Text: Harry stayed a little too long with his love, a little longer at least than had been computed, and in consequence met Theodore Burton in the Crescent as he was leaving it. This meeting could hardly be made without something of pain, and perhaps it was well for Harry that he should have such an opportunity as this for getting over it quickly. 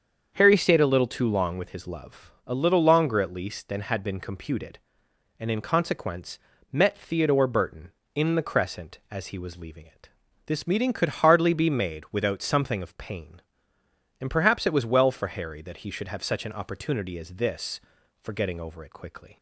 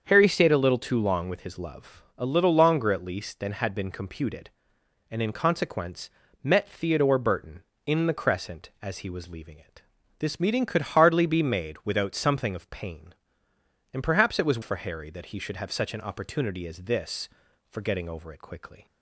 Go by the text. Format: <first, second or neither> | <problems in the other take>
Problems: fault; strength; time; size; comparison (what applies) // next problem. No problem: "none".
first | starts louder than the rest; strong; until 1.1 s; 7 dB; strong in the first // pauses between "consequence" and "met"; slight; at 6.1 s; 0.32 s long; slight in the first // skips "well"; at 14.6 s